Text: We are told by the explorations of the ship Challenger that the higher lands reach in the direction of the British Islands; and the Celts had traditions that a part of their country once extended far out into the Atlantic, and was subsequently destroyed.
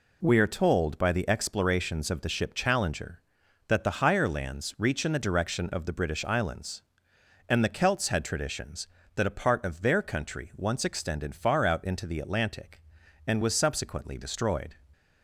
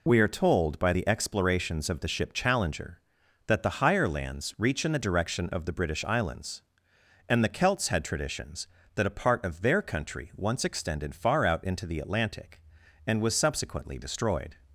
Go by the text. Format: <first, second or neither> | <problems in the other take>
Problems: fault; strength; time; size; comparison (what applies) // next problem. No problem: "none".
first | loses the start of "We"; at 0.0 s; 40 ms